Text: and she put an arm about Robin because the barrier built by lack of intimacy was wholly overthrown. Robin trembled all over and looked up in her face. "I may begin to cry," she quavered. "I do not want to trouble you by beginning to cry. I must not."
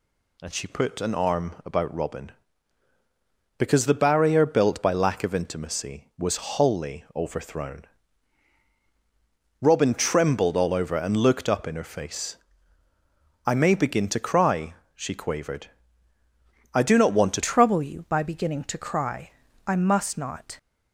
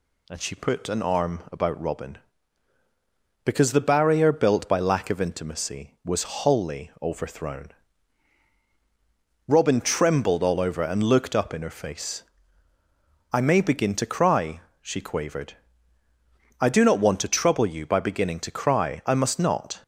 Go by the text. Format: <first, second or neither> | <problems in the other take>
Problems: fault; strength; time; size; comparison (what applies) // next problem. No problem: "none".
second | changes voice at "trouble"; from 17.4 s on; 3.1 s long